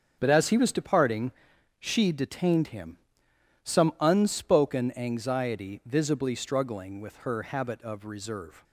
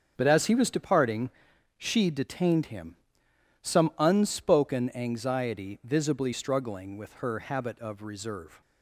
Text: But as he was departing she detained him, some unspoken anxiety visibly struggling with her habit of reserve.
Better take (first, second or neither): neither